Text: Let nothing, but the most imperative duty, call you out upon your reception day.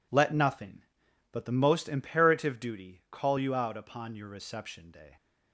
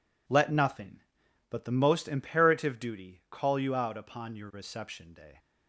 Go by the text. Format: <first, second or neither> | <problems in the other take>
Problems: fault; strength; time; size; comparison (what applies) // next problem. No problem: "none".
neither | none